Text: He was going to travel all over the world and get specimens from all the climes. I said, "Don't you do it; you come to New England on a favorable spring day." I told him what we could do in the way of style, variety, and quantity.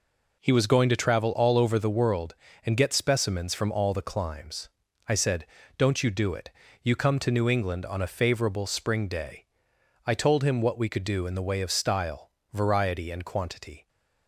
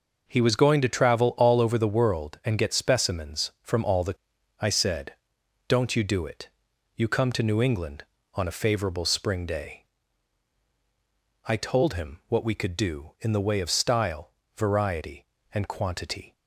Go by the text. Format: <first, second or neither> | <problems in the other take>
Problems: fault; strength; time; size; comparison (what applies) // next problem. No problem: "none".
first | skips "climes"; at 4.3 s